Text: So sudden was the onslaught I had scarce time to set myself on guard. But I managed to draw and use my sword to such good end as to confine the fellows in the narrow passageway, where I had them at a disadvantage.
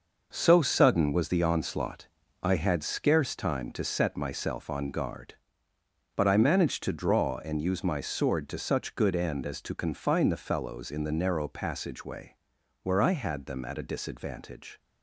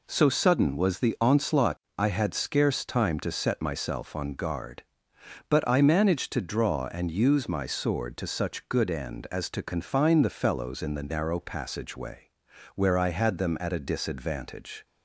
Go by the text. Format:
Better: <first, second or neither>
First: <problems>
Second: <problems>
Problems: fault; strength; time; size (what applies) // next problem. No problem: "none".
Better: second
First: gets quieter; strong; throughout; 8.5 dB // pauses between "onslaught" and "I"; slight; at 2.0 s; 0.34 s long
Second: pauses between "onslaught" and "I"; slight; at 1.7 s; 0.20 s long